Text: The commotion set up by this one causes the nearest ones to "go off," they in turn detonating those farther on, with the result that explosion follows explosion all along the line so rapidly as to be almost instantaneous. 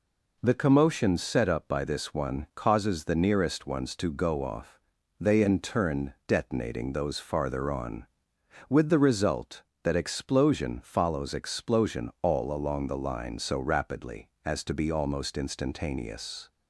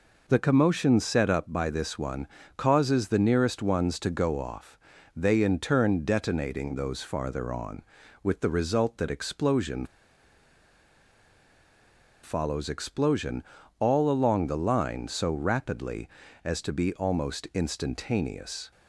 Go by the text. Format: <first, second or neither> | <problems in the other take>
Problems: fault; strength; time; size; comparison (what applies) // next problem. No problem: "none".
first | pauses between "one" and "causes"; slight; at 2.2 s; 0.30 s long // pauses between "explosion" and "follows"; strong; at 9.8 s; 2.3 s long // pauses between "explosion" and "all"; slight; at 13.4 s; 0.36 s long